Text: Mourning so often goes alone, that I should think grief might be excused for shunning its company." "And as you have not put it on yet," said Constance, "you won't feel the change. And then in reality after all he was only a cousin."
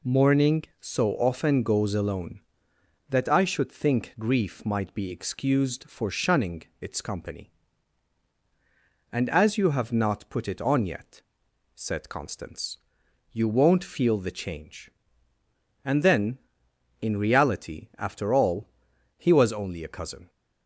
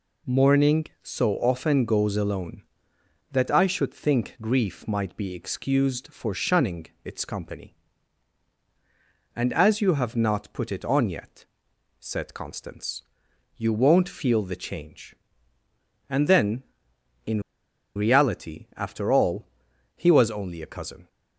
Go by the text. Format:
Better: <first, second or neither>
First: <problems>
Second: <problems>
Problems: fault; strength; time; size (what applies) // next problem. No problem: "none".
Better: first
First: pauses between "shunning" and "its"; slight; at 6.6 s; 0.18 s long // pauses between "all" and "he"; noticeable; at 18.6 s; 0.48 s long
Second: pauses between "shunning" and "its"; slight; at 6.8 s; 0.18 s long // pauses between "in" and "reality"; noticeable; at 17.4 s; 0.53 s long // pauses between "all" and "he"; noticeable; at 19.4 s; 0.48 s long